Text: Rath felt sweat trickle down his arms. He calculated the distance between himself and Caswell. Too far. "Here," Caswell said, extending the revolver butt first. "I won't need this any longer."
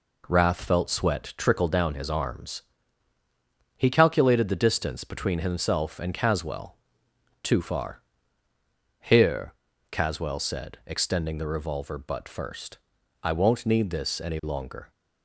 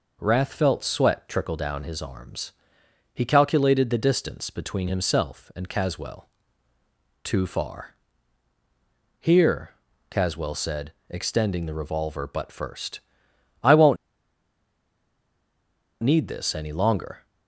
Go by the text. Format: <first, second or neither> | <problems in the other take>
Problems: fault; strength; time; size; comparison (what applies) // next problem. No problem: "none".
first | pauses between "won't" and "need"; strong; at 13.9 s; 2.0 s long